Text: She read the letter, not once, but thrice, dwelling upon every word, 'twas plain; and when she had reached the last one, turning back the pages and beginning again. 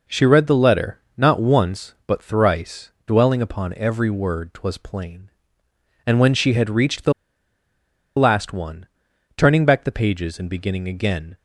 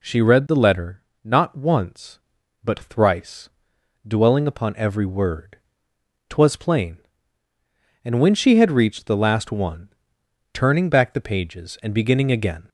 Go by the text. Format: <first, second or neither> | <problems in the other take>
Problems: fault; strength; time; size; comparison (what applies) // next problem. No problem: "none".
second | pauses between "the" and "last"; at 7.1 s; 1.0 s long